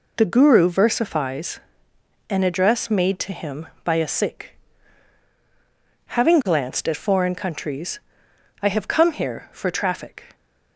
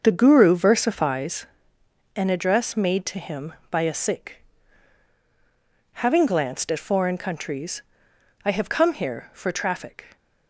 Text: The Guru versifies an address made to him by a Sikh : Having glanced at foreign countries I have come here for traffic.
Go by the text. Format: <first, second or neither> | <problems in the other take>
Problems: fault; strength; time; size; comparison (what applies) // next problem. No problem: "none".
first | starts louder than the rest; until 1.5 s; 6.5 dB // pauses between "versifies" and "an"; noticeable; at 1.4 s; 0.70 s long; noticeable in the first // pauses between "countries" and "I"; noticeable; at 7.8 s; 0.60 s long; noticeable in the first